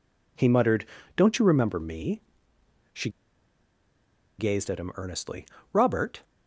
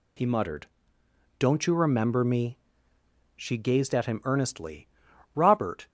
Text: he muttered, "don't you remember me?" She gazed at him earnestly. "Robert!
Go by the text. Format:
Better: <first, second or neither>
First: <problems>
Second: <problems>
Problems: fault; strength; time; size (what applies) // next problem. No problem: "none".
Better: second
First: pauses between "She" and "gazed"; strong; at 3.0 s; 1.2 s long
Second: none